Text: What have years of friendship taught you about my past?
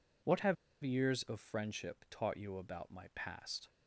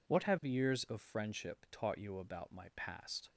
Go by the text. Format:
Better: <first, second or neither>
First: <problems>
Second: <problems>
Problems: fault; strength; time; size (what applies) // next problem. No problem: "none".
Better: second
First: pauses between "have" and "years"; slight; at 0.5 s; 0.27 s long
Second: none